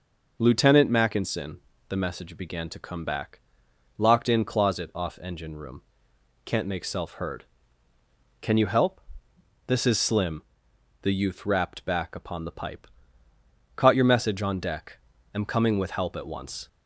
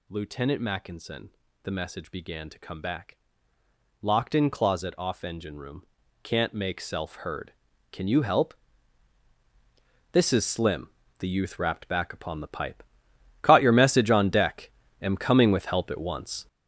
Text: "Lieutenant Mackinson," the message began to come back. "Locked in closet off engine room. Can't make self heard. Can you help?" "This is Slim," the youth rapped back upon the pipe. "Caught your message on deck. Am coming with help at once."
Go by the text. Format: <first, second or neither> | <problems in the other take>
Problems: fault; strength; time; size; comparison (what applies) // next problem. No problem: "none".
first | gets louder; strong; throughout; 8 dB